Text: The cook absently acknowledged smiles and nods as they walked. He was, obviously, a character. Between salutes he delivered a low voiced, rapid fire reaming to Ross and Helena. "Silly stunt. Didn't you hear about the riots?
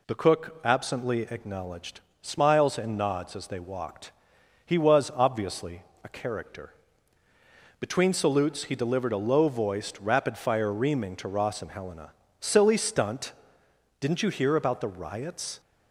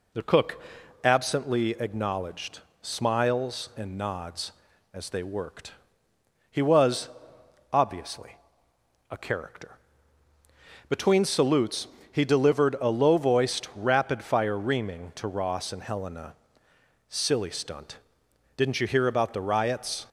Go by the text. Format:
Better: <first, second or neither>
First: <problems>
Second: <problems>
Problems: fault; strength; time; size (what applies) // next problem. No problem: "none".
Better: first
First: pauses between "acknowledged" and "smiles"; slight; at 2.0 s; 0.18 s long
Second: pauses between "cook" and "absently"; at 0.6 s; 0.44 s long // pauses between "acknowledged" and "smiles"; slight; at 2.6 s; 0.20 s long // says "worked" for "walked"; at 5.2 s // pauses between "salutes" and "he"; slight; at 11.8 s; 0.24 s long